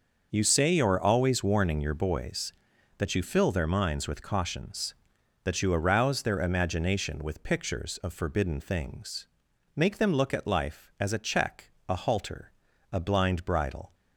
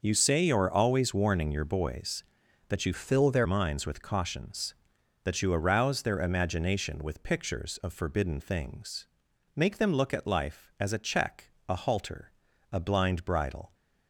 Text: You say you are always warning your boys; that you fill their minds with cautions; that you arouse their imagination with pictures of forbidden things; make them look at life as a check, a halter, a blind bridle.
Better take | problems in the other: first | starts louder than the rest; noticeable; until 1.0 s; 6 dB // changes voice from "fill" to "their"; from 2.9 to 3.4 s; 0.5 s long

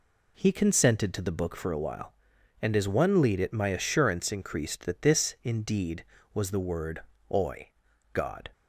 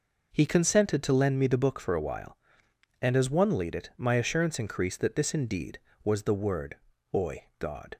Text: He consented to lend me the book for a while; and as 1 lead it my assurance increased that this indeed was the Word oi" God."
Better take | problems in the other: second | skips "lend me"; at 1.2 s // pauses between "Word" and "oi"; slight; at 6.9 s; 0.32 s long; slight in the second // pauses between "oi" and "God"; at 7.6 s; 0.42 s long

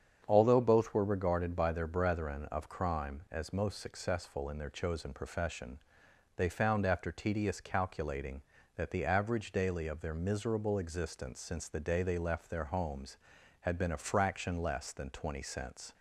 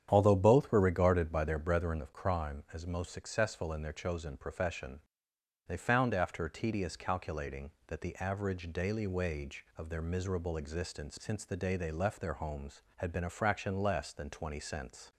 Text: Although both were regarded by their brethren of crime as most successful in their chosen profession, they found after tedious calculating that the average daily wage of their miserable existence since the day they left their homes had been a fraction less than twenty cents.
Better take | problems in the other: second | starts louder than the rest; strong; until 1.2 s; 7.5 dB; strong in the second // skips "wage"; at 9.8 s

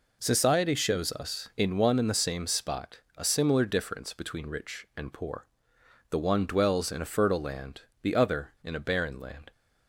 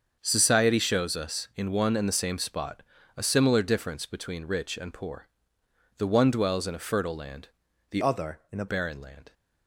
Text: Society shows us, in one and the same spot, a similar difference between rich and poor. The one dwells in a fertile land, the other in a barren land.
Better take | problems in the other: first | starts louder than the rest; until 1.2 s; 7 dB // changes voice from "other" to "a"; from 8.0 to 8.6 s; 0.6 s long

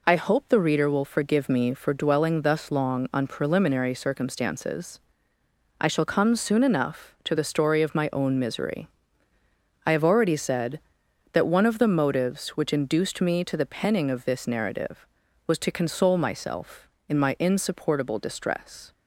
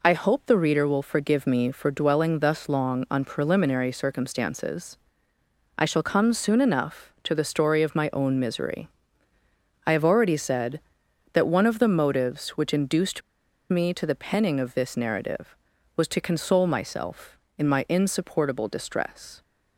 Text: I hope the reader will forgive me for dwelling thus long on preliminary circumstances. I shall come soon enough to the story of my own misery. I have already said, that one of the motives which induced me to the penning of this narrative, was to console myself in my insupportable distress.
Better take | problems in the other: first | pauses between "induced" and "me"; noticeable; at 13.2 s; 0.50 s long

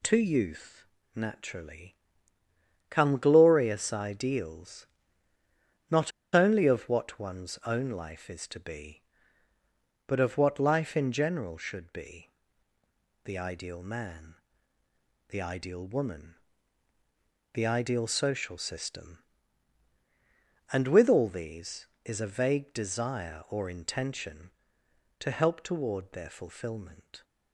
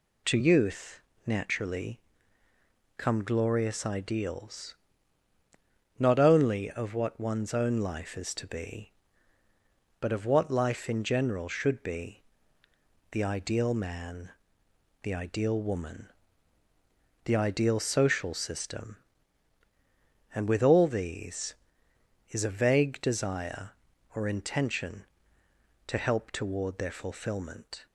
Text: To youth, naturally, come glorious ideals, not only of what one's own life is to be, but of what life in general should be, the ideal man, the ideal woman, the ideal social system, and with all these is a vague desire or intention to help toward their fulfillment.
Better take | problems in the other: second | pauses between "not" and "only"; slight; at 6.1 s; 0.22 s long

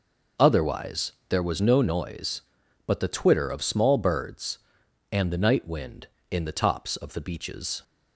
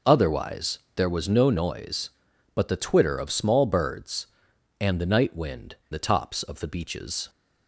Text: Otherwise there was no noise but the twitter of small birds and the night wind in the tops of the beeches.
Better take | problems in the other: first | pauses between "Otherwise" and "there"; slight; at 0.7 s; 0.16 s long; slight in the first // skips "in"; at 5.8 s

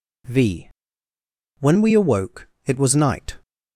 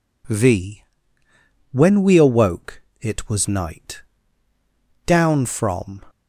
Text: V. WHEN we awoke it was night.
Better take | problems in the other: first | pauses between "awoke" and "it"; slight; at 2.8 s; 0.18 s long; slight in the first // goes on to say "Down from"; noticeable; from 5.0 s on; 0.98 s long

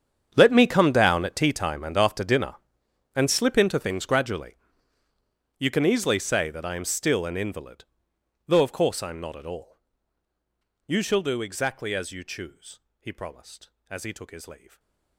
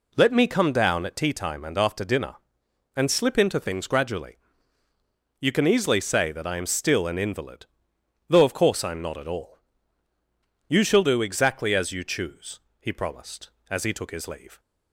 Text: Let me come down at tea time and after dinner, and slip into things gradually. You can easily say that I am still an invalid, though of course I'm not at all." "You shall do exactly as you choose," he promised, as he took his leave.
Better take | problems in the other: second | gets quieter; strong; throughout; 19 dB // stays silent after the last word; slight; from 14.6 s on; 0.5 s long

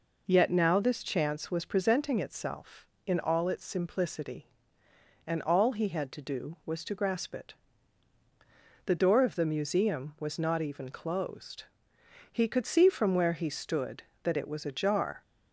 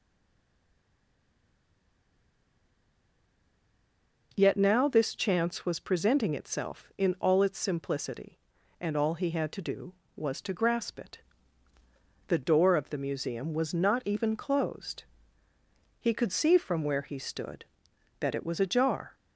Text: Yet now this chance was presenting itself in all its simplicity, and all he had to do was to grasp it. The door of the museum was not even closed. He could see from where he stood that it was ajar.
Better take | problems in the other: first | stays silent before the first word; strong; until 4.3 s; 4.3 s long

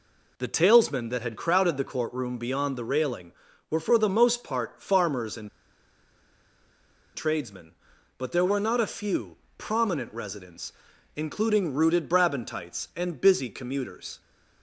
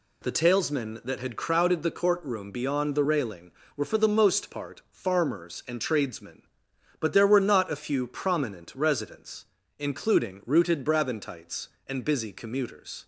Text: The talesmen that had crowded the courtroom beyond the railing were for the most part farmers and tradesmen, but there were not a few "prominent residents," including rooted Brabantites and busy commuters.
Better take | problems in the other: second | pauses between "and" and "tradesmen"; strong; at 5.4 s; 1.6 s long // pauses between "few" and "prominent"; slight; at 9.3 s; 0.22 s long

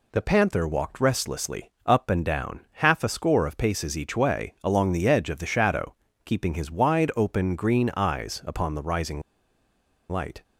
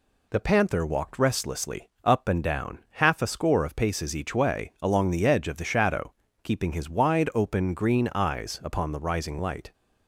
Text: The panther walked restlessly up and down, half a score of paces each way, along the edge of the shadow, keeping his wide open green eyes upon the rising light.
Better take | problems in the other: second | pauses between "restlessly" and "up"; slight; at 1.6 s; 0.16 s long; slight in the second // pauses between "rising" and "light"; noticeable; at 9.2 s; 0.89 s long

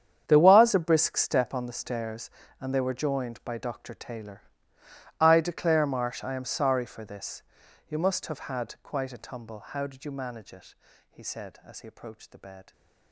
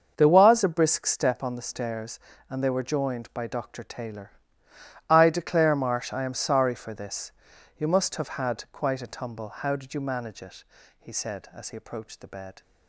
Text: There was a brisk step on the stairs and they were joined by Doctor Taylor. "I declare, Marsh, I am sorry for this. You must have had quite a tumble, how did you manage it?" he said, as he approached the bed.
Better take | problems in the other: second | gets quieter; strong; throughout; 16 dB // starts louder than the rest; strong; until 1.3 s; 8.5 dB; also in the second

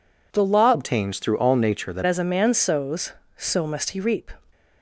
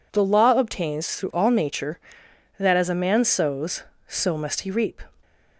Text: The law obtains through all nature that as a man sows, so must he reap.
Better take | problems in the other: second | changes voice from "obtains" to "that"; from 0.7 to 2.0 s; 1.3 s long

